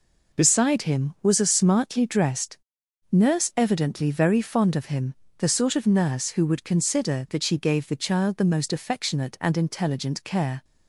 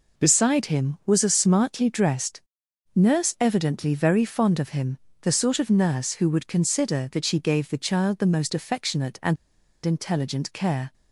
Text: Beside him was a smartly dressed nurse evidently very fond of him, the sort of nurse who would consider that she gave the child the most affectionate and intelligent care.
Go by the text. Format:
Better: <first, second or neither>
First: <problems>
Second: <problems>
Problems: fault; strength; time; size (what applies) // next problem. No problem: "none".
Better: first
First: pauses between "dressed" and "nurse"; noticeable; at 2.5 s; 0.58 s long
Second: pauses between "dressed" and "nurse"; noticeable; at 2.3 s; 0.58 s long // pauses between "and" and "intelligent"; noticeable; at 9.3 s; 0.48 s long